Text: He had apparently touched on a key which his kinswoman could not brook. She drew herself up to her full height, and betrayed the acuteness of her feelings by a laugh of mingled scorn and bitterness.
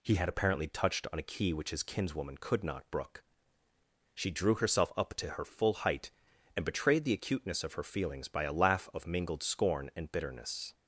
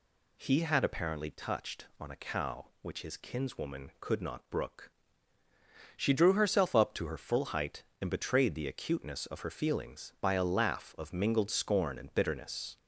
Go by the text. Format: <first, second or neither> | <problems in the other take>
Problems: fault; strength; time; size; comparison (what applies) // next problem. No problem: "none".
first | says "cow" for "key"; at 2.1 s